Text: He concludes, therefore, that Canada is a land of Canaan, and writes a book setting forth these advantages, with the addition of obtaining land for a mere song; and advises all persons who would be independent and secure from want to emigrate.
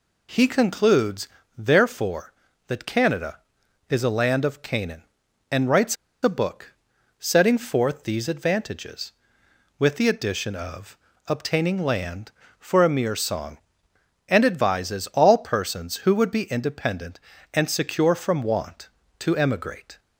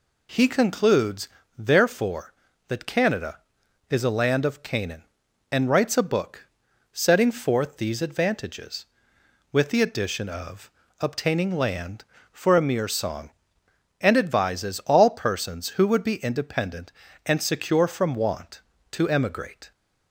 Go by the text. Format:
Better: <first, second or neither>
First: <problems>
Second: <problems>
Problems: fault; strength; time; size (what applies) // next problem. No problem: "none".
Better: second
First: pauses between "writes" and "a"; slight; at 5.9 s; 0.28 s long // pauses between "book" and "setting"; noticeable; at 6.7 s; 0.46 s long // pauses between "of" and "obtaining"; slight; at 10.9 s; 0.30 s long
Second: pauses between "book" and "setting"; noticeable; at 6.4 s; 0.46 s long // pauses between "of" and "obtaining"; slight; at 10.7 s; 0.29 s long